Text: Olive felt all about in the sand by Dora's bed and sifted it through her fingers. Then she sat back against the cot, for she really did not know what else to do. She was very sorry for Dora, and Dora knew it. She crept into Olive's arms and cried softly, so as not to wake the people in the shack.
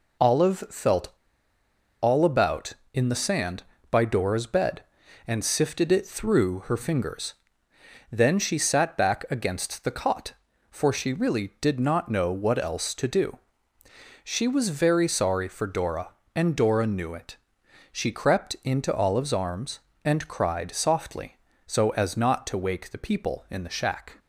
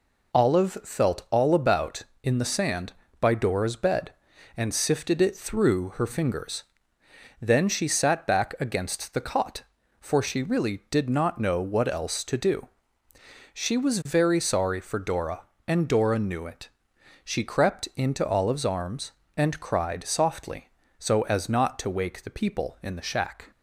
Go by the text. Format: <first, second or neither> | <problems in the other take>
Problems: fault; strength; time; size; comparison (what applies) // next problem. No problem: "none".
second | pauses between "felt" and "all"; noticeable; at 1.1 s; 0.90 s long